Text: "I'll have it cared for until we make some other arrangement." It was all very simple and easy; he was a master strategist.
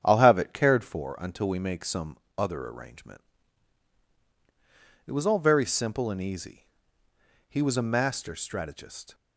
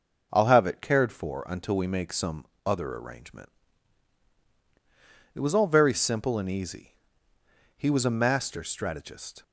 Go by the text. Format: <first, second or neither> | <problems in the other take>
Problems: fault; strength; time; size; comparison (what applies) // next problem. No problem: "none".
second | starts louder than the rest; strong; until 1.1 s; 8.5 dB // pauses between "some" and "other"; slight; at 2.1 s; 0.20 s long; slight in the second